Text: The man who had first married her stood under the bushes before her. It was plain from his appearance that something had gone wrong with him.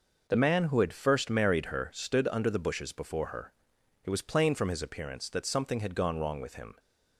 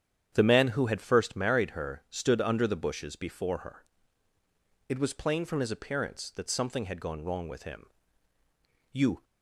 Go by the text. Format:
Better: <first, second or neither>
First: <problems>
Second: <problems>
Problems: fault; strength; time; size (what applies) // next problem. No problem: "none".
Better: first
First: none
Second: starts louder than the rest; strong; until 1.3 s; 9 dB // goes on to say "You"; slight; from 8.9 s on; 0.32 s long